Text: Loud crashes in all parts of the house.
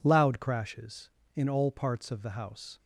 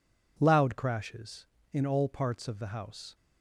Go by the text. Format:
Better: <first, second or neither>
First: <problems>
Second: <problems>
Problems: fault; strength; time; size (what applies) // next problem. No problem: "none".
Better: neither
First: none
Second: none